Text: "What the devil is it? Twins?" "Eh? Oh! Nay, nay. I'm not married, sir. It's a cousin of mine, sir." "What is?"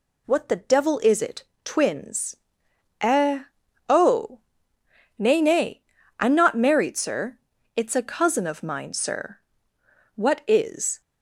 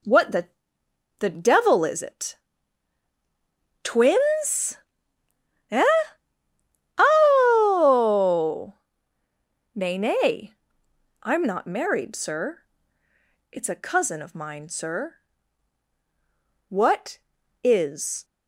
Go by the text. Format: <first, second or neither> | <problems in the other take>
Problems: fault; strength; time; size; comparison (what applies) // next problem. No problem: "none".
first | says "the" twice; at 1.2 s